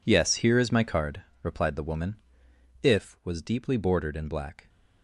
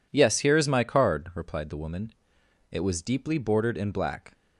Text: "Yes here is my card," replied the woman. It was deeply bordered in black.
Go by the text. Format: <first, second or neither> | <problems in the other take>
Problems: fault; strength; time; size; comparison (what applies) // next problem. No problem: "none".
second | says "If" for "It"; at 2.8 s